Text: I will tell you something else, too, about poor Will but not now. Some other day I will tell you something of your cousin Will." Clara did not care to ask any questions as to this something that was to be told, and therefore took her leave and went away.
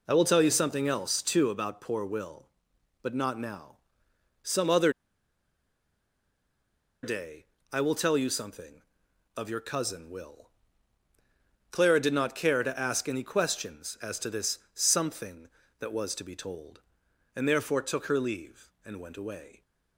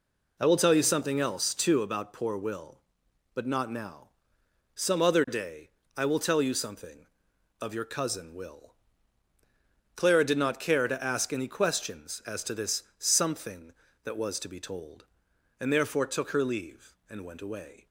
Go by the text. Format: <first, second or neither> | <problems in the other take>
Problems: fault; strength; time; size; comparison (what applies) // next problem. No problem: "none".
second | pauses between "other" and "day"; strong; at 4.9 s; 2.1 s long // pauses between "day" and "I"; slight; at 7.4 s; 0.26 s long; slight in the second // pauses between "this" and "something"; slight; at 14.5 s; 0.16 s long; slight in the second